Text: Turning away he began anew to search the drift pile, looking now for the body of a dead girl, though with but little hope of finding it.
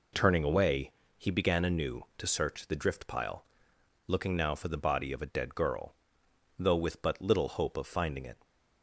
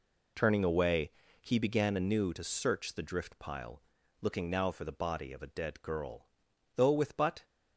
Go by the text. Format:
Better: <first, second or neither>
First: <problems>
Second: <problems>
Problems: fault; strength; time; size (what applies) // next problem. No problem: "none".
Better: first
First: pauses between "away" and "he"; slight; at 0.9 s; 0.26 s long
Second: pauses between "away" and "he"; slight; at 1.0 s; 0.32 s long // stops before "little hope of finding it"; at 7.4 s